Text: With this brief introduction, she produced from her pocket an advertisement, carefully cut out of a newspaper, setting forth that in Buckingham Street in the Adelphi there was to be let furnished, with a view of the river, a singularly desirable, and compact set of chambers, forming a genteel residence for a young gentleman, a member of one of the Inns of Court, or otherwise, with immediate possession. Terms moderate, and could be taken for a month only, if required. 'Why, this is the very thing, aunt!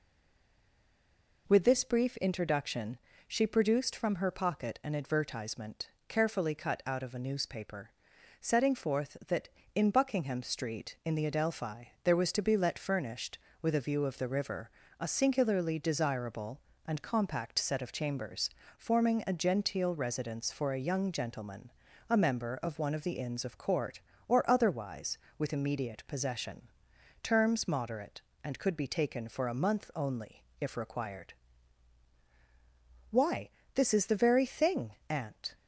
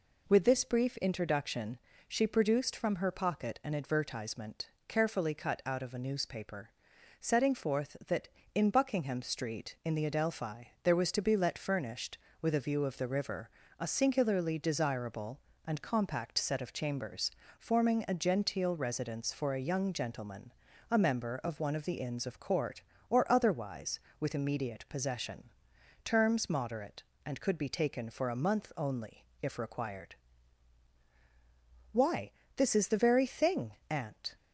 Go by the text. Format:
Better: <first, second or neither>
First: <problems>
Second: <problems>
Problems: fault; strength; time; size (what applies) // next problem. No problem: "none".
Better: second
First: stays silent before the first word; noticeable; until 1.4 s; 1.4 s long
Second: none